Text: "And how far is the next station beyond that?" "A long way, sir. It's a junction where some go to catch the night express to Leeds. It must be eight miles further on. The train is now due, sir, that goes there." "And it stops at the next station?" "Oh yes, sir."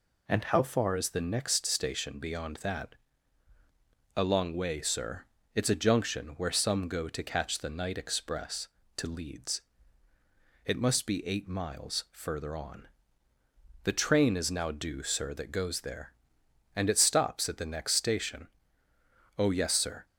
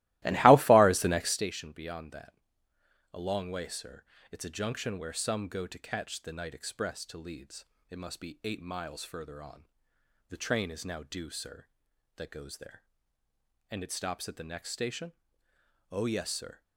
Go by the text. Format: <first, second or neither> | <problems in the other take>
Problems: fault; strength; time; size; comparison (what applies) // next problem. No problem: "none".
first | starts louder than the rest; strong; until 1.4 s; 18 dB